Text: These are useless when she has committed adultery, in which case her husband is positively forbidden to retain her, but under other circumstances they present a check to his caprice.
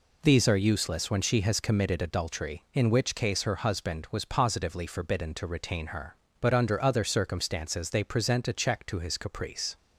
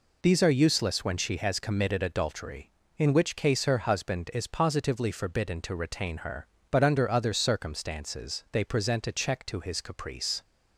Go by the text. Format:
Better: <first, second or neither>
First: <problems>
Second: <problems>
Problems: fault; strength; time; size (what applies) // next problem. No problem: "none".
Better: second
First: says "was" for "is"; at 4.1 s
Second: none